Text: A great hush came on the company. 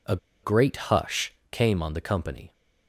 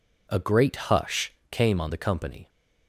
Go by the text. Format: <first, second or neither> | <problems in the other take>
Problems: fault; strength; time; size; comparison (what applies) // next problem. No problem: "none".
second | pauses between "A" and "great"; slight; at 0.1 s; 0.26 s long // pauses between "hush" and "came"; slight; at 1.3 s; 0.18 s long; slight in the second